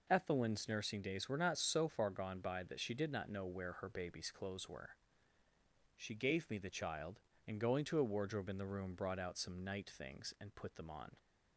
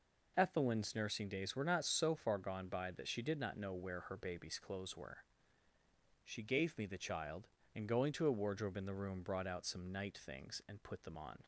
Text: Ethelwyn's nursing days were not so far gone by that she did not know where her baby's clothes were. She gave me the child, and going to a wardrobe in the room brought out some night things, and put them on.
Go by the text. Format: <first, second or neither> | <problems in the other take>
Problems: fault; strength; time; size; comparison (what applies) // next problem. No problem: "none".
neither | none